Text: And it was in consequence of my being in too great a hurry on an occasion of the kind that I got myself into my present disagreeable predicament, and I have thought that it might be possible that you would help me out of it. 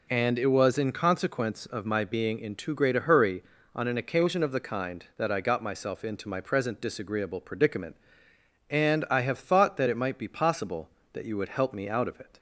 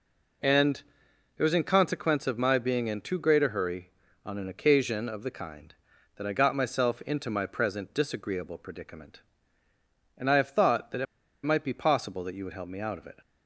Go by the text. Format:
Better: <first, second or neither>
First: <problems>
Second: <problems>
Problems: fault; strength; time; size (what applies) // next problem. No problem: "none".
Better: first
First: none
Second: pauses between "And" and "it"; noticeable; at 0.8 s; 0.56 s long // pauses between "it" and "might"; at 11.0 s; 0.38 s long